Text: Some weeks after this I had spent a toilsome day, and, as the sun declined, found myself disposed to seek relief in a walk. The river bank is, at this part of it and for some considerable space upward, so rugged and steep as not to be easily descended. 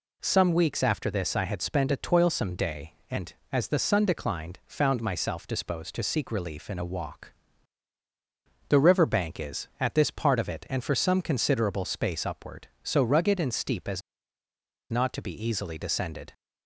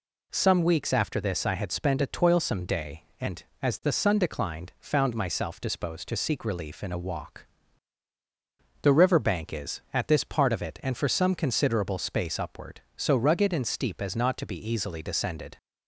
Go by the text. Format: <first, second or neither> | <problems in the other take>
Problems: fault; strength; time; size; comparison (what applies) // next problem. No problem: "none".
second | pauses between "as" and "not"; noticeable; at 14.0 s; 0.89 s long